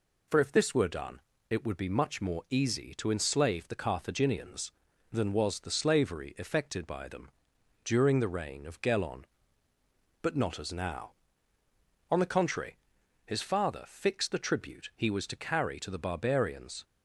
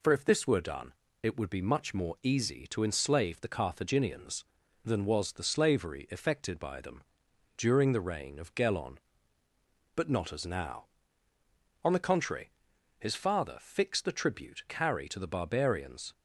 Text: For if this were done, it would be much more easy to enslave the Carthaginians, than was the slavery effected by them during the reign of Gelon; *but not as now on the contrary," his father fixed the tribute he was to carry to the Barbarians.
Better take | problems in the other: first | pauses between "them" and "during"; noticeable; at 7.0 s; 0.56 s long; noticeable in the first // skips "he was to"; at 14.6 s

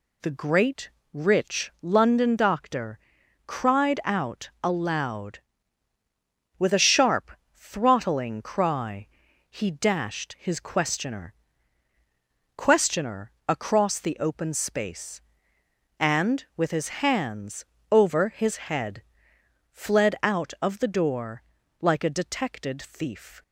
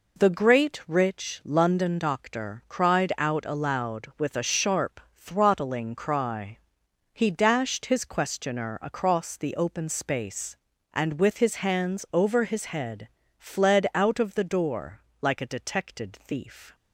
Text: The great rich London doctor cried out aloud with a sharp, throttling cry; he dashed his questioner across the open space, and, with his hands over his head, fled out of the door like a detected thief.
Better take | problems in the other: second | pauses between "great" and "rich"; slight; at 0.9 s; 0.24 s long // pauses between "doctor" and "cried"; noticeable; at 2.9 s; 0.48 s long // says "questioner" twice; at 12.5 s // pauses between "hands" and "over"; slight; at 17.6 s; 0.26 s long // pauses between "door" and "like"; at 21.4 s; 0.38 s long; slight in the second

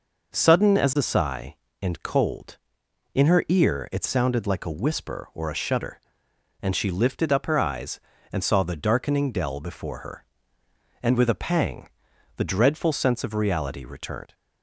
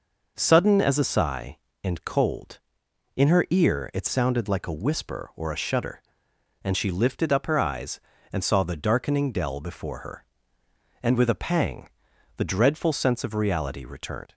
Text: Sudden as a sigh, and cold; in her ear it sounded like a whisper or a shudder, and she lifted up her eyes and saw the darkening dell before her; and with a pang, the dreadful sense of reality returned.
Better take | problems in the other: neither | none

